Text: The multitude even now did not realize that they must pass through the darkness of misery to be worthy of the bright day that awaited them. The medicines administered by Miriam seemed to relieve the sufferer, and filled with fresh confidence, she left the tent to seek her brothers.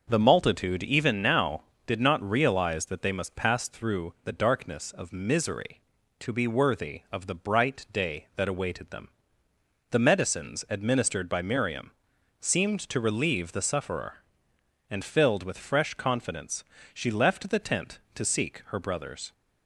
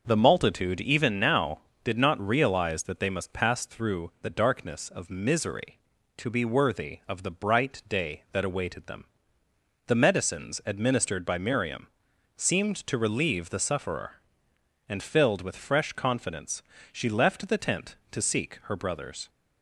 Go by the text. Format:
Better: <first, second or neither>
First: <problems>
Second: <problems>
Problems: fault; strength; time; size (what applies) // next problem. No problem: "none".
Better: neither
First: starts louder than the rest; until 1.0 s; 6 dB // pauses between "Miriam" and "seemed"; noticeable; at 11.9 s; 0.50 s long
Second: starts louder than the rest; until 1.0 s; 6 dB // pauses between "Miriam" and "seemed"; noticeable; at 11.8 s; 0.50 s long